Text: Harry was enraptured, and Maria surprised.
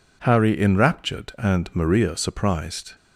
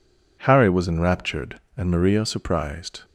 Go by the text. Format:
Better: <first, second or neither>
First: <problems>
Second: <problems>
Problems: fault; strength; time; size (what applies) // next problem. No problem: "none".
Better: second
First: skips "was"; at 0.5 s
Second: none